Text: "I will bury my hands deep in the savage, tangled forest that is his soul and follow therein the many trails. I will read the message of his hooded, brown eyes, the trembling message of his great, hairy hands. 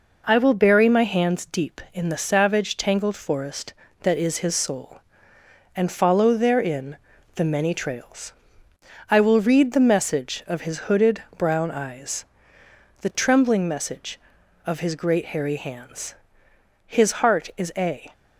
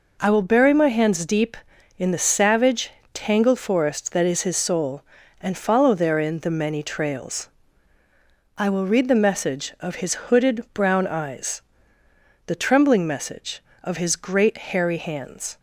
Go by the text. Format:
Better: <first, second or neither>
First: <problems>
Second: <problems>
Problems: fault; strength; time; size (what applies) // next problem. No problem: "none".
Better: second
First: pauses between "therein" and "the"; at 6.9 s; 0.38 s long // goes on to say "His heart is a"; noticeable; from 16.8 s on; 1.2 s long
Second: none